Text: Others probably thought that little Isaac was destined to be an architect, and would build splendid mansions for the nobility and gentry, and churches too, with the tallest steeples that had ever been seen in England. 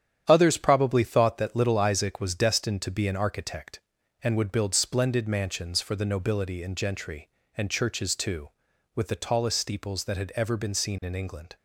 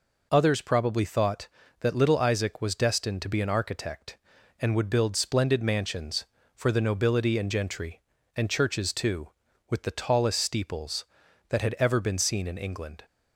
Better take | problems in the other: second | gets quieter; throughout; 7 dB

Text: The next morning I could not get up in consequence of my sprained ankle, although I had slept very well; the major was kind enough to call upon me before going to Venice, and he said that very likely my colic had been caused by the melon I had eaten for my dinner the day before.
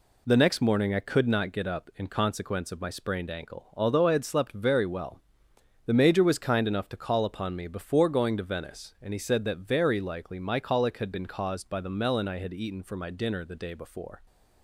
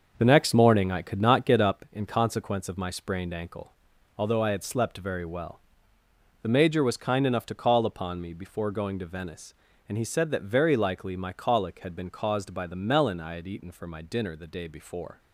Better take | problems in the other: first | starts louder than the rest; until 1.9 s; 6.5 dB

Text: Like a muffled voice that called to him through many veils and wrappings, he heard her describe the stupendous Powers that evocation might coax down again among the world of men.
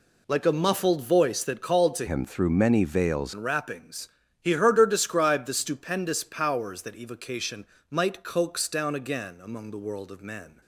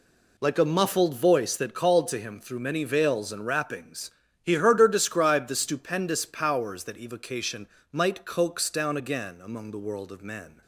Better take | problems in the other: second | changes voice from "him" to "veils"; from 2.0 to 3.3 s; 1.3 s long // pauses between "evocation" and "might"; slight; at 7.6 s; 0.24 s long; slight in the second

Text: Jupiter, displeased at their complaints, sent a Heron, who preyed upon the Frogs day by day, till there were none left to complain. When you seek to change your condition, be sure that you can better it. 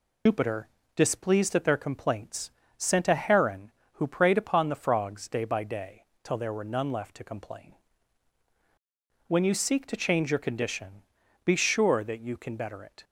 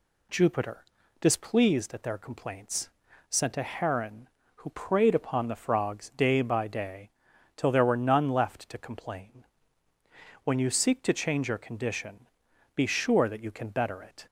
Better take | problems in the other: second | loses the start of "Jupiter"; at 0.2 s; 100 ms

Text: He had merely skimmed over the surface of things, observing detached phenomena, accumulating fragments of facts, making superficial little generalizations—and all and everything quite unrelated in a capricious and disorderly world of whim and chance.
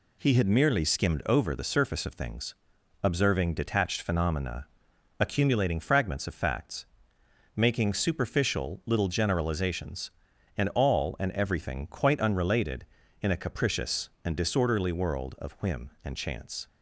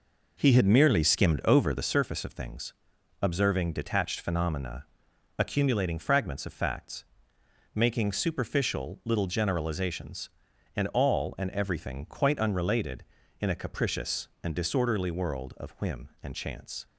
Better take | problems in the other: first | starts louder than the rest; noticeable; until 2.0 s; 4.5 dB

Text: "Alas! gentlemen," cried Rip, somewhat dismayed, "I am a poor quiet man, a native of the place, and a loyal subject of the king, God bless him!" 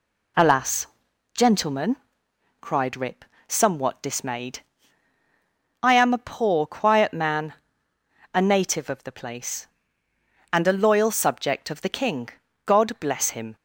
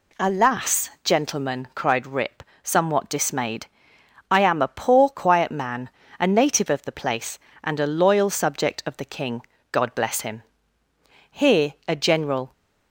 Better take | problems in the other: first | goes on to say "Here a general"; noticeable; from 11.3 s on; 1.2 s long

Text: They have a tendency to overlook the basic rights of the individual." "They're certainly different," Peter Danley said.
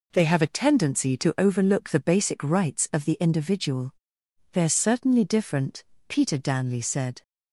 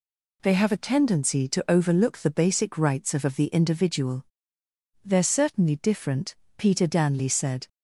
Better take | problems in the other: first | says "of" twice; at 3.2 s

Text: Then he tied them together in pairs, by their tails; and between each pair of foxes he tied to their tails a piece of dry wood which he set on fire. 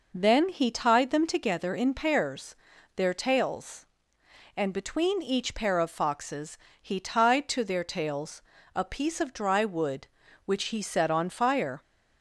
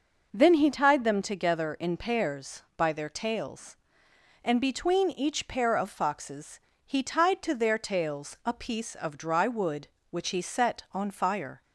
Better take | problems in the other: second | skips "by"; at 2.7 s // pauses between "foxes" and "he"; slight; at 6.5 s; 0.20 s long; slight in the second // pauses between "tails" and "a"; slight; at 8.4 s; 0.32 s long

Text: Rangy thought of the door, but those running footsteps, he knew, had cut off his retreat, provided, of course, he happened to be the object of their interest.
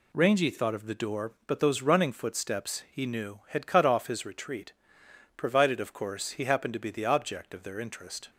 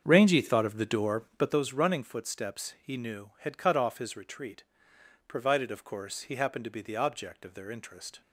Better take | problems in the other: first | starts louder than the rest; strong; until 1.6 s; 7 dB

